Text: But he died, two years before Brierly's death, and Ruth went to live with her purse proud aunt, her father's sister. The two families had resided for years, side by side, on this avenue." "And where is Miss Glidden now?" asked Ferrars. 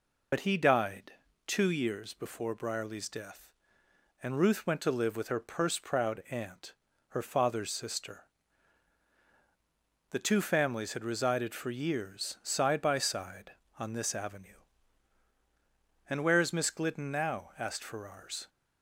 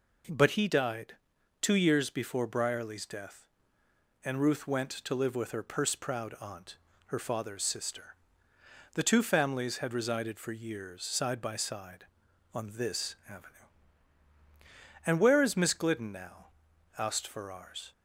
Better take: second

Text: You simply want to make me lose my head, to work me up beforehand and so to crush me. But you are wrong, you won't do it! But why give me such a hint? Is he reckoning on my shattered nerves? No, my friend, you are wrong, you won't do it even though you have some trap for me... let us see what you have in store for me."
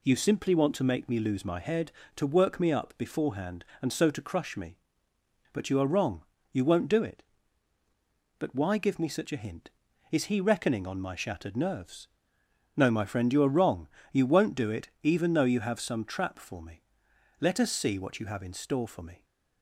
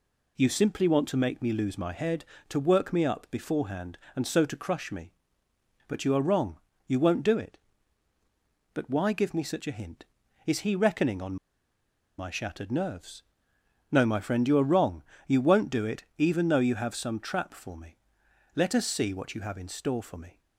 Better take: first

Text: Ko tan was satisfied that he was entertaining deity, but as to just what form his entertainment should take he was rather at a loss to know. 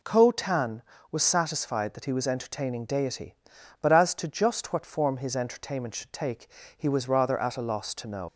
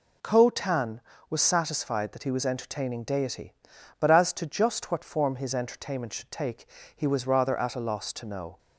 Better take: second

